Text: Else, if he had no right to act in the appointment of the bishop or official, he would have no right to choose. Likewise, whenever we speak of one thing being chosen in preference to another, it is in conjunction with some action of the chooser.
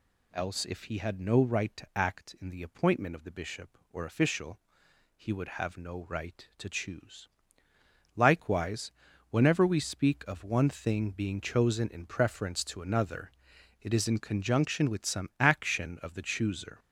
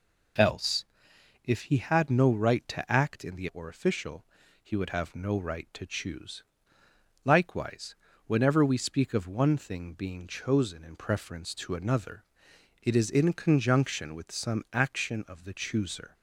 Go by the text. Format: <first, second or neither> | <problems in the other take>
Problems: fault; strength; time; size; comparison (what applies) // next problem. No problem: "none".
first | skips "appointment of the bishop"; at 3.5 s